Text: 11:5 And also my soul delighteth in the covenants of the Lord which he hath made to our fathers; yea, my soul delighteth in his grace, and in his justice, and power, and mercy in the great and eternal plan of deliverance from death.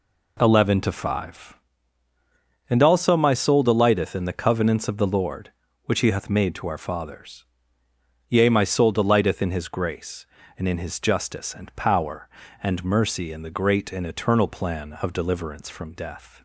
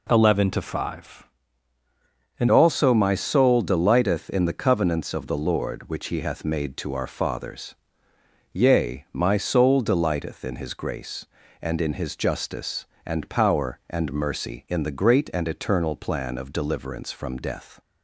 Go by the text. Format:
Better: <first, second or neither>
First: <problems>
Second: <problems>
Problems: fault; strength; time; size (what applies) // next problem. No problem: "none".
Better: first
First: none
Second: changes voice at "also"; from 2.4 s on; 15.3 s long